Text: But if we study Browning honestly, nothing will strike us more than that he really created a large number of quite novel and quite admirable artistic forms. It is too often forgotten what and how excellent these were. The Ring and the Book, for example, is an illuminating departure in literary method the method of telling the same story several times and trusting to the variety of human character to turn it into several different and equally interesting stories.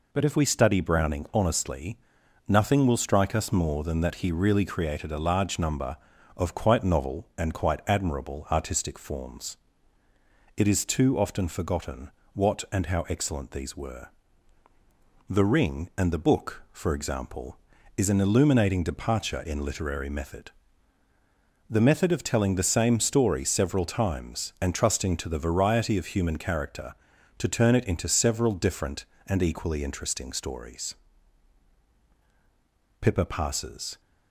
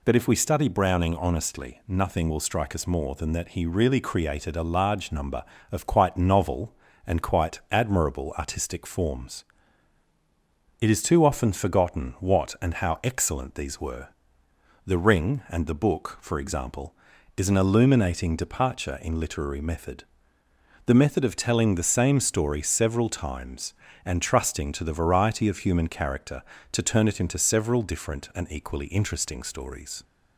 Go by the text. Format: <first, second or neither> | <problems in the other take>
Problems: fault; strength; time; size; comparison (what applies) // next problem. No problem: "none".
second | pauses between "forgotten" and "what"; slight; at 12.1 s; 0.22 s long // pauses between "method" and "the"; at 20.5 s; 1.2 s long; noticeable in the second // goes on to say "Pippa Passes"; noticeable; from 33.0 s on; 1.0 s long